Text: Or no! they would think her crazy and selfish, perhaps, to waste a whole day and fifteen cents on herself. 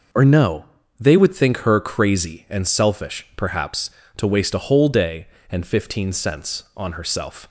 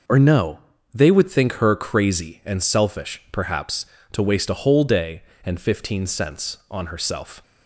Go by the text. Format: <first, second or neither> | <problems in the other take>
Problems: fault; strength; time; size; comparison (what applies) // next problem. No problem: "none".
neither | none